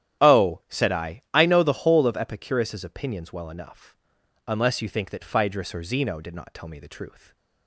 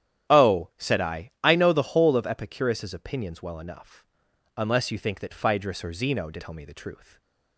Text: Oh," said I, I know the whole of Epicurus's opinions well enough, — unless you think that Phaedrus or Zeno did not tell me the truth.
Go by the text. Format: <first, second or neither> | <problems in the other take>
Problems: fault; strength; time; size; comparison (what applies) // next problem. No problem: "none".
first | starts louder than the rest; strong; until 1.5 s; 11 dB; strong in the first // skips "not"; at 6.4 s // stays silent after the last word; slight; from 7.0 s on; 0.5 s long